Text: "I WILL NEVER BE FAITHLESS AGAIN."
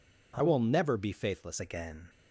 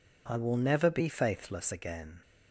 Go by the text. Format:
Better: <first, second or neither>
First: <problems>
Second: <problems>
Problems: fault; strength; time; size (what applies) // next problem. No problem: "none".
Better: second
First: changes voice from "WILL" to "FAITHLESS"; from 0.4 to 1.5 s; 1.1 s long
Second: none